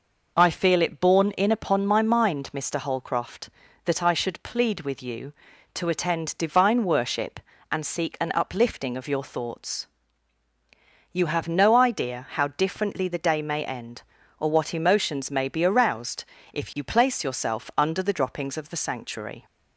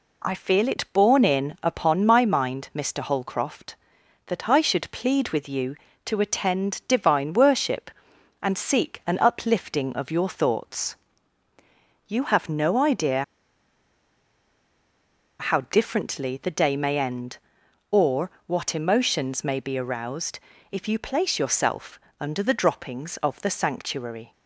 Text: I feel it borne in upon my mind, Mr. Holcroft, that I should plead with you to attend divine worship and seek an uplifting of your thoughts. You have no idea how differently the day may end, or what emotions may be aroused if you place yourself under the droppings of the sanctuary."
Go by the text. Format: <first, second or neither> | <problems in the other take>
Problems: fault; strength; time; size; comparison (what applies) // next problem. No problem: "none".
first | pauses between "idea" and "how"; strong; at 13.2 s; 2.1 s long // pauses between "or" and "what"; slight; at 18.2 s; 0.16 s long // pauses between "aroused" and "if"; slight; at 20.3 s; 0.32 s long; slight in the first // pauses between "yourself" and "under"; slight; at 21.9 s; 0.22 s long